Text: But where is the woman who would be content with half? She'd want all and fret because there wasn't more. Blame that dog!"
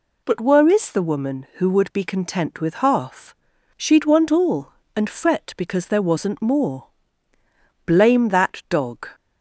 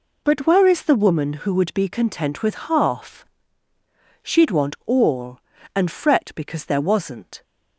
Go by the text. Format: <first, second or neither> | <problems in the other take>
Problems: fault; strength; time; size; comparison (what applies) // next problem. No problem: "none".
first | stops before "more Blame that dog"; at 7.4 s